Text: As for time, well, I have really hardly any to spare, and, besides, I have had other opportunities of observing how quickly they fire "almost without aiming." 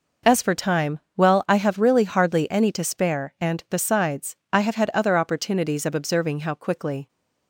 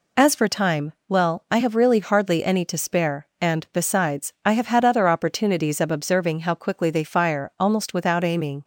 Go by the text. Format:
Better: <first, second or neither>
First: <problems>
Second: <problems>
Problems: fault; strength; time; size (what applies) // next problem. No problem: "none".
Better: second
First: stops before "they fire almost without aiming"; at 7.0 s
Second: none